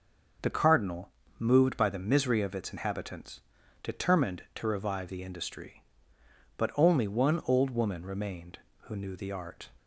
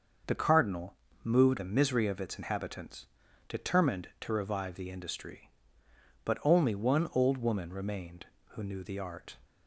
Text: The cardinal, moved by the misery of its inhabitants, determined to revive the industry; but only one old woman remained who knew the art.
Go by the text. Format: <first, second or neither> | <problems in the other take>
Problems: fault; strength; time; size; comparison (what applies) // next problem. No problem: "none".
first | starts louder than the rest; until 1.5 s; 6 dB // skips "by"; at 1.5 s